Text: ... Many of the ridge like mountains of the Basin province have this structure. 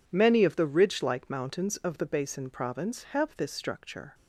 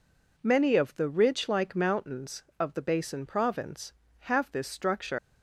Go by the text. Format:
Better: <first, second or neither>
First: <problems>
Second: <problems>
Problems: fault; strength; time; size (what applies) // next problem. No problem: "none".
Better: first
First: none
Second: leaves "structure" unfinished; at 5.1 s; 110 ms